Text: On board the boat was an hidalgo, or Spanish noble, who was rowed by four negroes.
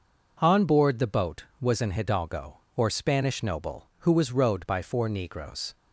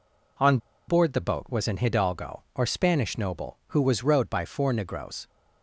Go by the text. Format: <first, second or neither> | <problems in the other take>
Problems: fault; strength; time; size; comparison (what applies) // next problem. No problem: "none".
first | pauses between "On" and "board"; slight; at 0.5 s; 0.30 s long